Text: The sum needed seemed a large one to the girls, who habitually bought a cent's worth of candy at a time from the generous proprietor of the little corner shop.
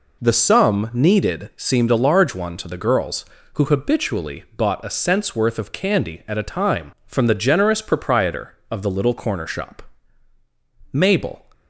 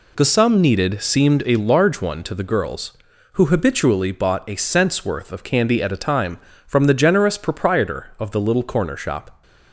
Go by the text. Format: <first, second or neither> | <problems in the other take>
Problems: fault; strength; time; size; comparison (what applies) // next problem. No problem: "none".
second | goes on to say "Mabel"; from 10.9 s on; 0.54 s long